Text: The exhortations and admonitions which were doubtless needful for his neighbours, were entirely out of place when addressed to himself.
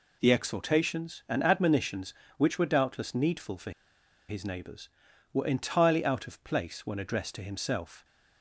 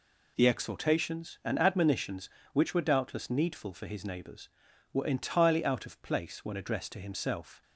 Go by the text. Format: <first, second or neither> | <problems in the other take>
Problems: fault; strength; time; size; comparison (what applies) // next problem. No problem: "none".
second | pauses between "for" and "his"; noticeable; at 3.7 s; 0.58 s long